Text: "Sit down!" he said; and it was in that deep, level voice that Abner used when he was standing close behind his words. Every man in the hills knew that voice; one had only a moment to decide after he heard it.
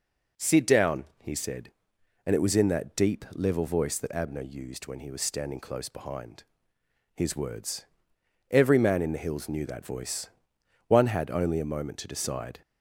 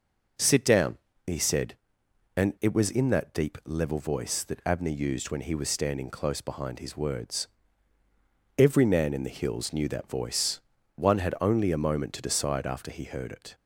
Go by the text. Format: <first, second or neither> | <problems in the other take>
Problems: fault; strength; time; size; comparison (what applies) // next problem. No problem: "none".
second | pauses between "behind" and "his"; noticeable; at 6.4 s; 0.72 s long // stops before "after he heard it"; at 12.6 s